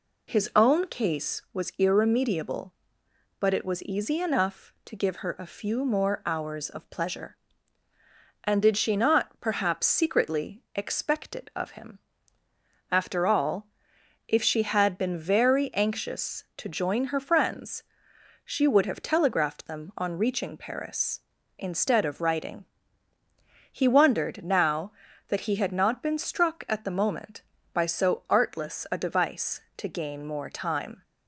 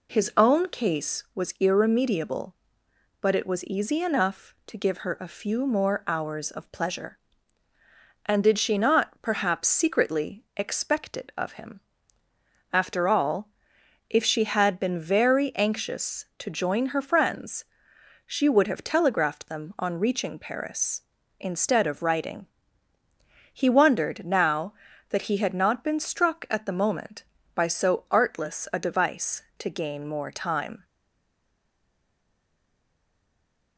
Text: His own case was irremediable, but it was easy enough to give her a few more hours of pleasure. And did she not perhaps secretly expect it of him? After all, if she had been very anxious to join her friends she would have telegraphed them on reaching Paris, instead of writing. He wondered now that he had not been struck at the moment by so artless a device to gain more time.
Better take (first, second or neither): first